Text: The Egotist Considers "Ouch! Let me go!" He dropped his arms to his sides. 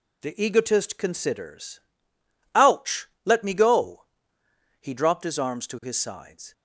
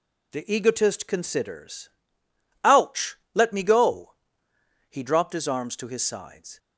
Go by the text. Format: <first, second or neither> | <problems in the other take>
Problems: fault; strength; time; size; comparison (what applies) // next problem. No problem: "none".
neither | pauses between "Considers" and "Ouch"; noticeable; the same in both